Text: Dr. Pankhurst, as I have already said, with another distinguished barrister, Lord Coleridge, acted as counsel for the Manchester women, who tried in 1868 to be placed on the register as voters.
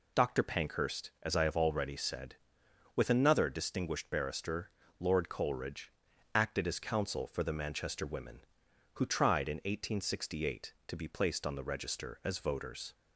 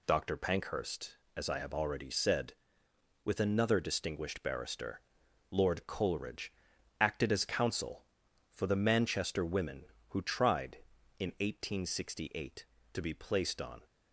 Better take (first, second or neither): first